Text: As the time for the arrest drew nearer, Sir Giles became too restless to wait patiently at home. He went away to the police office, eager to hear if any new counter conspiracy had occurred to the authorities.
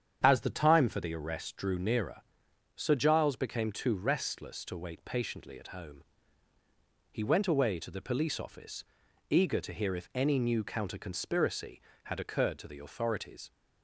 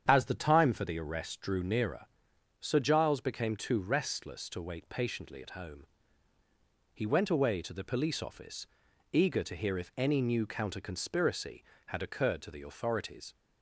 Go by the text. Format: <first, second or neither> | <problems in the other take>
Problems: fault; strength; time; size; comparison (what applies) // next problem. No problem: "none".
neither | starts louder than the rest; strong; the same in both